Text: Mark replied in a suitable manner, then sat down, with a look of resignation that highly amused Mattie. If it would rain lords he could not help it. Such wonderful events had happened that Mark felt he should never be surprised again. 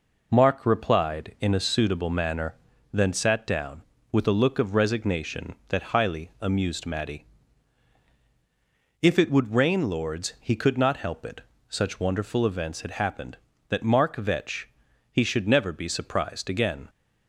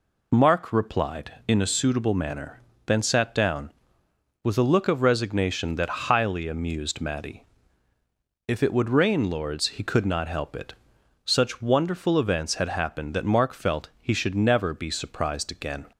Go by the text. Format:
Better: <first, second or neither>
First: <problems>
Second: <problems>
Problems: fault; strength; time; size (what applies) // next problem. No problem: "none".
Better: second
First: says "vetch" for "felt"; at 14.1 s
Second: none